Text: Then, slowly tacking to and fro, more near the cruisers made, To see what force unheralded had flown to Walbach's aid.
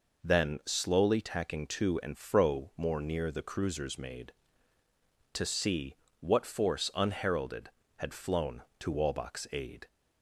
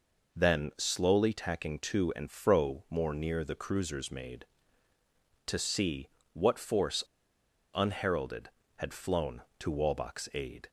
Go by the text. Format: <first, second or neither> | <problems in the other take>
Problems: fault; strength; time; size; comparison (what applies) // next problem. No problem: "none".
first | pauses between "see" and "what"; slight; at 6.0 s; 0.24 s long; slight in the first // pauses between "force" and "unheralded"; noticeable; at 7.0 s; 0.72 s long